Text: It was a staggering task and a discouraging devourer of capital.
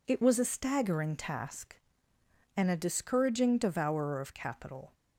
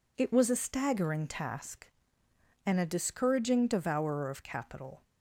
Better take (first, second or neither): neither